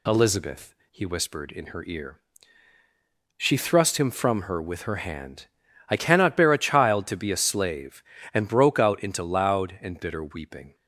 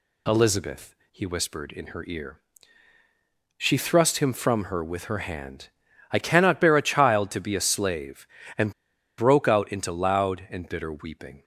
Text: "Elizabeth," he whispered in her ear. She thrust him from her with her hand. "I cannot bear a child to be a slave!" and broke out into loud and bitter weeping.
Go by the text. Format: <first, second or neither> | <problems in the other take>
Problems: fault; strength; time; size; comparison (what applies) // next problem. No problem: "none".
first | pauses between "and" and "broke"; at 8.7 s; 0.45 s long